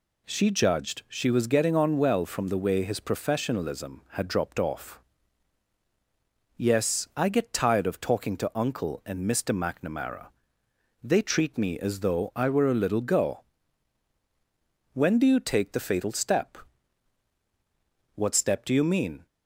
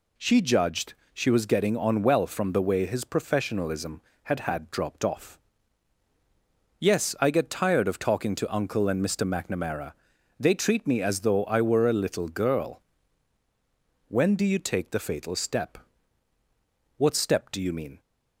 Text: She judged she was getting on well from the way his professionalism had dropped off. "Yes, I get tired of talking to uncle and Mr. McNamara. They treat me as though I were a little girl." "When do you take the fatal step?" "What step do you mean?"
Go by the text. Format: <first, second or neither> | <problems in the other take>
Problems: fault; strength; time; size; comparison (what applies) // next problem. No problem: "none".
first | pauses between "judged" and "she"; slight; at 0.9 s; 0.20 s long // says "had" twice; at 4.3 s